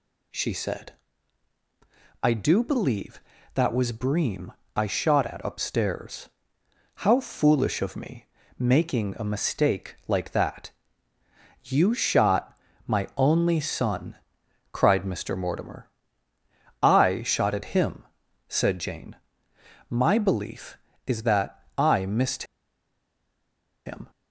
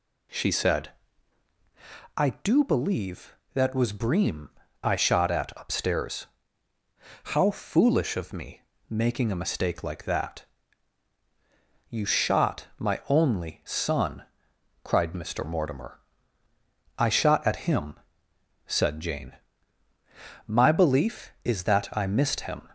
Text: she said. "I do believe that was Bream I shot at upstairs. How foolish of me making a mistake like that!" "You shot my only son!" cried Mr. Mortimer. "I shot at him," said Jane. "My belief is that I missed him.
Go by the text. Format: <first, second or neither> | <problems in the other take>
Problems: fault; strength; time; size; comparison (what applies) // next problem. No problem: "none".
second | pauses between "Bream" and "I"; slight; at 4.5 s; 0.24 s long; slight in the second // pauses between "me" and "making"; slight; at 8.2 s; 0.32 s long; slight in the second // pauses between "shot" and "my"; slight; at 12.5 s; 0.30 s long // pauses between "missed" and "him"; strong; at 22.4 s; 1.4 s long